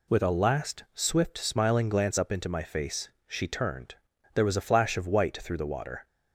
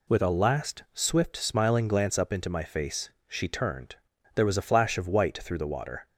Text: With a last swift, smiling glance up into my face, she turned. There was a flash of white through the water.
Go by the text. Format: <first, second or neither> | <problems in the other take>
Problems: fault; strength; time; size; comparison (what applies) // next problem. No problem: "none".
neither | none